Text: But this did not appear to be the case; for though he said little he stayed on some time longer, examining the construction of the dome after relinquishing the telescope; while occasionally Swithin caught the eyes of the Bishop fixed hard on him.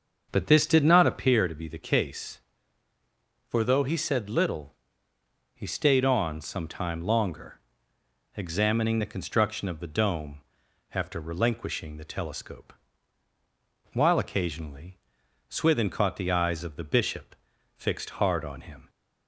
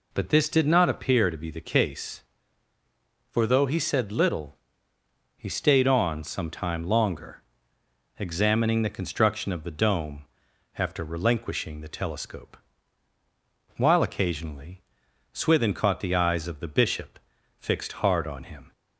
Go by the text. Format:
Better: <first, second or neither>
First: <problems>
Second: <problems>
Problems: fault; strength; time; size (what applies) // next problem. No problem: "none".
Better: second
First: starts louder than the rest; until 1.5 s; 6.5 dB // pauses between "little" and "he"; noticeable; at 4.7 s; 0.80 s long // pauses between "dome" and "after"; noticeable; at 10.4 s; 0.52 s long // pauses between "occasionally" and "Swithin"; noticeable; at 14.9 s; 0.50 s long // pauses between "Bishop" and "fixed"; at 17.3 s; 0.44 s long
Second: pauses between "little" and "he"; noticeable; at 4.5 s; 0.80 s long // pauses between "dome" and "after"; noticeable; at 10.2 s; 0.52 s long // pauses between "occasionally" and "Swithin"; noticeable; at 14.8 s; 0.50 s long // pauses between "Bishop" and "fixed"; at 17.1 s; 0.42 s long